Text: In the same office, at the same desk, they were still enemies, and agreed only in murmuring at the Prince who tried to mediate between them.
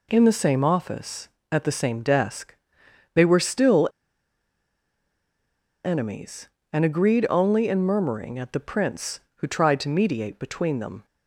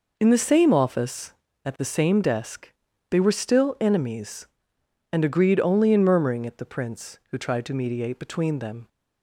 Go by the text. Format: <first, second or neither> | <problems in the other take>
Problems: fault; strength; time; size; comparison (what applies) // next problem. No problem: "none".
second | pauses between "still" and "enemies"; strong; at 3.8 s; 1.9 s long